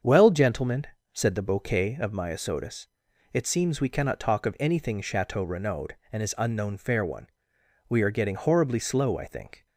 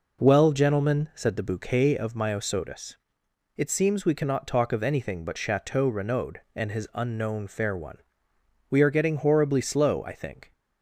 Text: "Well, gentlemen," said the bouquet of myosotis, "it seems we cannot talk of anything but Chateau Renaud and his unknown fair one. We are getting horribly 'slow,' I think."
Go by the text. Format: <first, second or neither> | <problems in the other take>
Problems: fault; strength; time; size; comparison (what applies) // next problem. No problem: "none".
second | starts louder than the rest; strong; until 1.3 s; 7 dB // skips "but"; at 5.0 s